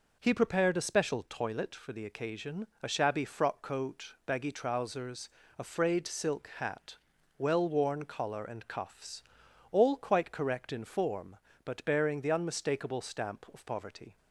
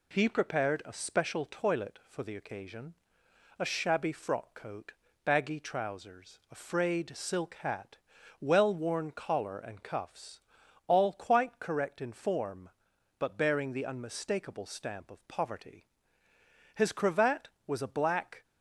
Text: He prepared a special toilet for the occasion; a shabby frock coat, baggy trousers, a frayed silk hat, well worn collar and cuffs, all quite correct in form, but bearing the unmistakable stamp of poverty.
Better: first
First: none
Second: goes on to say "His cravat was a black"; strong; from 16.7 s on; 1.7 s long

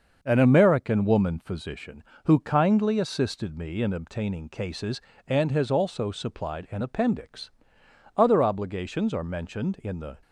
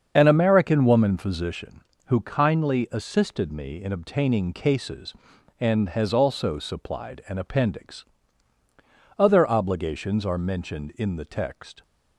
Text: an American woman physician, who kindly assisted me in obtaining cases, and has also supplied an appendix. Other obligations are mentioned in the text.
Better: second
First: starts louder than the rest; until 1.2 s; 6.5 dB // stops before "text"; at 10.2 s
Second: starts louder than the rest; until 1.2 s; 7 dB

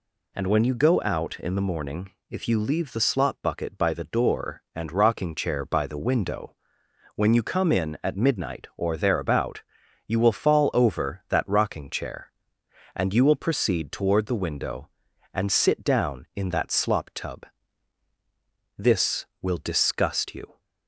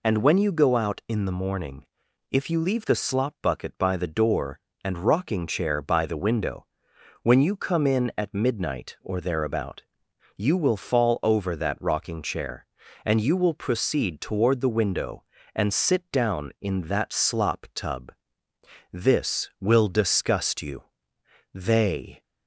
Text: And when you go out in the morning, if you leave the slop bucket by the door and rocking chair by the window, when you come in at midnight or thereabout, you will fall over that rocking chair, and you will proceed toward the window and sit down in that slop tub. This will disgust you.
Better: first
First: none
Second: goes on to say "They"; noticeable; from 21.5 s on; 0.70 s long

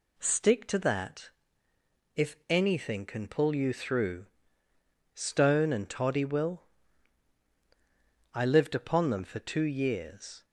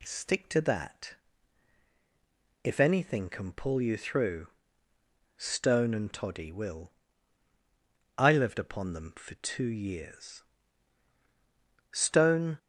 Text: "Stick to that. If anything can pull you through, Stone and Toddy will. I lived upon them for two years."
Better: first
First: none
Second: goes on to say "Stone"; noticeable; from 11.9 s on; 0.66 s long

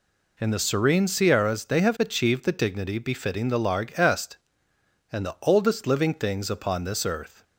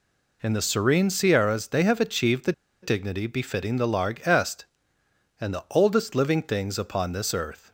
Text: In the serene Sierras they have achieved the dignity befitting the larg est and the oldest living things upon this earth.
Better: first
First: none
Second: pauses between "the" and "dignity"; slight; at 2.5 s; 0.30 s long

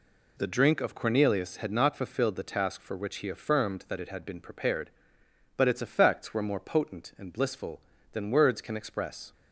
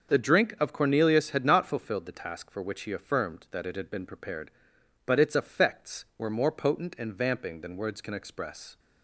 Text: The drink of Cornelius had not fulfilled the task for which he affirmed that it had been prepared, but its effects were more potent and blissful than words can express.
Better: first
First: none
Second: says "vamping" for "blissful"; at 7.1 s

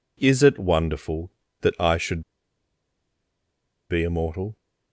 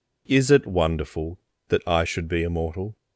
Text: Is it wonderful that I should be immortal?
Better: second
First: pauses between "should" and "be"; strong; at 2.2 s; 1.6 s long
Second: none

